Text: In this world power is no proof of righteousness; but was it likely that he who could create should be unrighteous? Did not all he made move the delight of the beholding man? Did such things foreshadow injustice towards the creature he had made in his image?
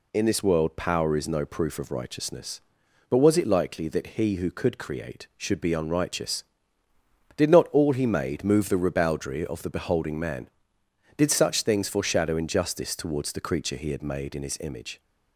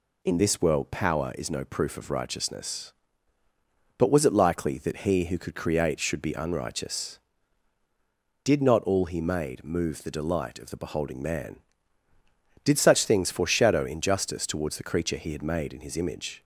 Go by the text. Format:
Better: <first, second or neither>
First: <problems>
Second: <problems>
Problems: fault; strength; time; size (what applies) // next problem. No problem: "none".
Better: second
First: says "ribaldry" for "delight"; at 8.7 s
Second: none